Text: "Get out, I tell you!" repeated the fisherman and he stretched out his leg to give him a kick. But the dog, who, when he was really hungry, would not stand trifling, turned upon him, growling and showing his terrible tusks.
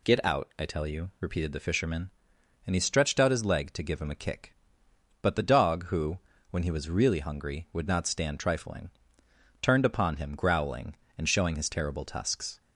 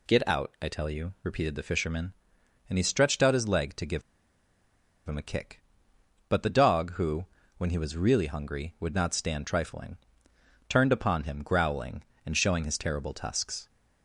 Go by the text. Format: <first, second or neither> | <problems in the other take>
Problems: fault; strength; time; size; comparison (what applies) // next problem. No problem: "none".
first | pauses between "give" and "him"; at 4.0 s; 1.0 s long